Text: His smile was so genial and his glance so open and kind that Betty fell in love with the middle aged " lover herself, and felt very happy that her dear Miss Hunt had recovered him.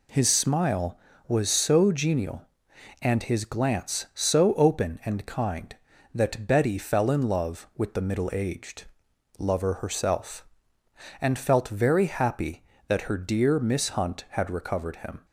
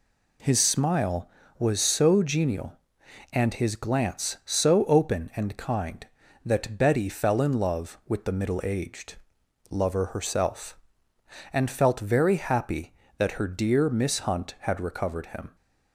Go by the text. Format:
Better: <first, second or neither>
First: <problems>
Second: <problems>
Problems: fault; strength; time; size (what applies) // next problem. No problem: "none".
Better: neither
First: none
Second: none